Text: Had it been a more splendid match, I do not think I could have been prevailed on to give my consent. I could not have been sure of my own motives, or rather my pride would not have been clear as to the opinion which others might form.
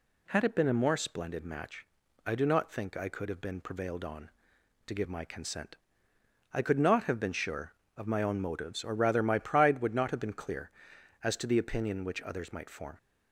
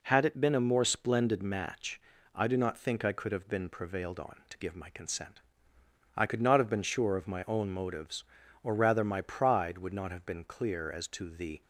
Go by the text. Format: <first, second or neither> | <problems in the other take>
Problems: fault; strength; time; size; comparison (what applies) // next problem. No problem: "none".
first | stops before "opinion which others might form"; at 11.6 s